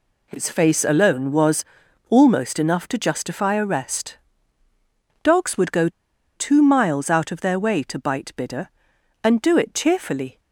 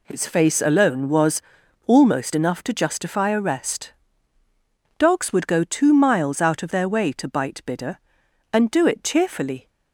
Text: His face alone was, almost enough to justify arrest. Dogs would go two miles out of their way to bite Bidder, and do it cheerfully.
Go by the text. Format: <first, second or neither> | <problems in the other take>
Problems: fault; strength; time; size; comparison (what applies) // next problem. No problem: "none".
second | pauses between "go" and "two"; noticeable; at 5.8 s; 0.46 s long